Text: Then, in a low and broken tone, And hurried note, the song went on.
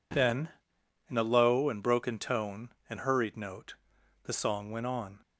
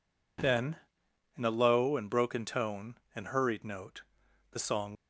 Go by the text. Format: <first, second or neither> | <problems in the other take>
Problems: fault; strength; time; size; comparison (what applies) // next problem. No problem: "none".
first | stops before "went on"; at 4.9 s